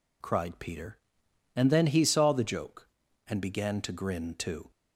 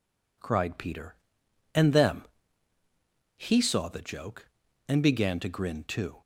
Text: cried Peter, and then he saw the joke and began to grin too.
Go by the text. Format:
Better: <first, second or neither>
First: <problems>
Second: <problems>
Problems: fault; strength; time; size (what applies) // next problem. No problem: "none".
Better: first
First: none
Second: says "them" for "then"; at 1.9 s